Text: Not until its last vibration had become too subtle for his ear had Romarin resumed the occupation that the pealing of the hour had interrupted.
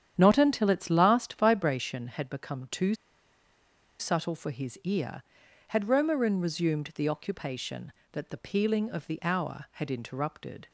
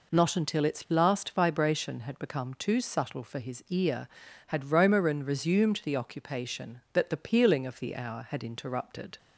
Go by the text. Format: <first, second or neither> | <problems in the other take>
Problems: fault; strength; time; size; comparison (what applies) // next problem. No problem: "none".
second | starts louder than the rest; strong; until 1.1 s; 9.5 dB // pauses between "too" and "subtle"; at 2.9 s; 1.0 s long